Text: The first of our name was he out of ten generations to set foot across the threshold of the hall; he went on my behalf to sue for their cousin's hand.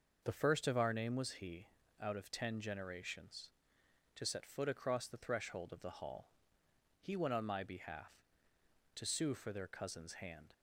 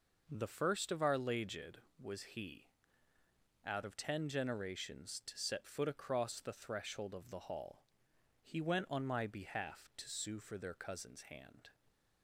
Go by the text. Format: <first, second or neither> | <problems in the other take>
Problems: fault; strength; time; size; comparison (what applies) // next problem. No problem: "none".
first | says "laged" for "name"; at 1.1 s // pauses between "he" and "out"; noticeable; at 2.6 s; 0.98 s long; slight in the first